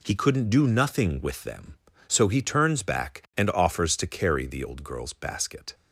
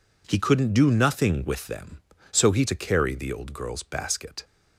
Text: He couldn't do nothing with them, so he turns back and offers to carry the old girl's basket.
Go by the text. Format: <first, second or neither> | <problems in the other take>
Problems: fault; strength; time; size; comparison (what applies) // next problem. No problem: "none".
first | skips "turns back and offers"; at 2.6 s